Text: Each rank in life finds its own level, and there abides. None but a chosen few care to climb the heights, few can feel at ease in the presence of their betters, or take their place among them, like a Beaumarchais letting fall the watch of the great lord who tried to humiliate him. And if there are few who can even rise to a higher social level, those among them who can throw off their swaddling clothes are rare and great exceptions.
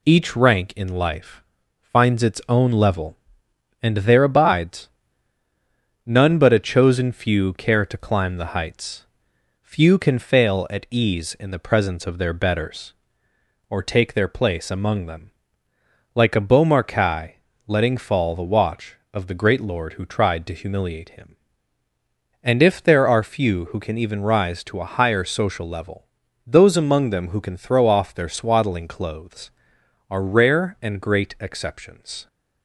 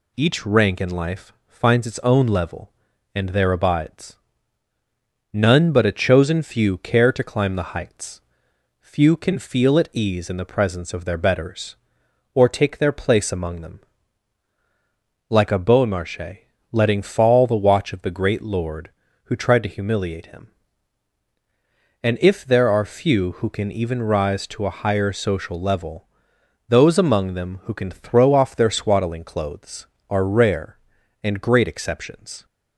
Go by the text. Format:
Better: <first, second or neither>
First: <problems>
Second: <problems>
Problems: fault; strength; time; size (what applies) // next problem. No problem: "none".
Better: second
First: pauses between "life" and "finds"; slight; at 1.4 s; 0.36 s long // says "fail" for "feel"; at 10.1 s // pauses between "Beaumarchais" and "letting"; slight; at 17.3 s; 0.32 s long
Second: pauses between "life" and "finds"; slight; at 1.3 s; 0.16 s long // pauses between "Beaumarchais" and "letting"; slight; at 16.4 s; 0.28 s long